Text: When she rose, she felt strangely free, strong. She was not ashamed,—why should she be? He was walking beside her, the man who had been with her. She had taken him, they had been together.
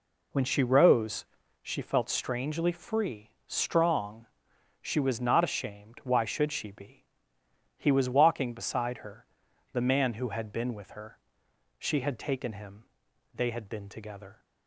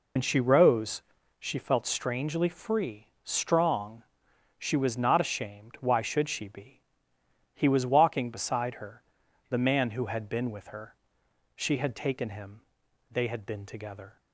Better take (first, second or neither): first